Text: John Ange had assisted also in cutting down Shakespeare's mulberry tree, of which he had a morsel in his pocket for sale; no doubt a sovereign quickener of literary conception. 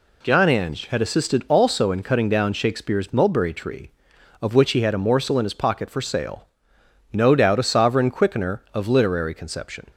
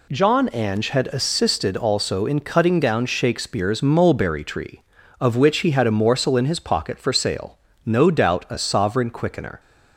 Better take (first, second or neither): first